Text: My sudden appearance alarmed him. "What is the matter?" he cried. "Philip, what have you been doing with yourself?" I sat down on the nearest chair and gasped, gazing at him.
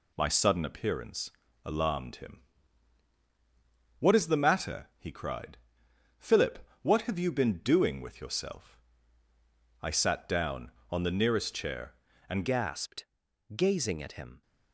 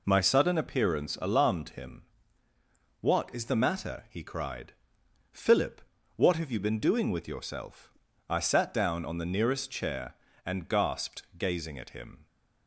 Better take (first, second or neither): second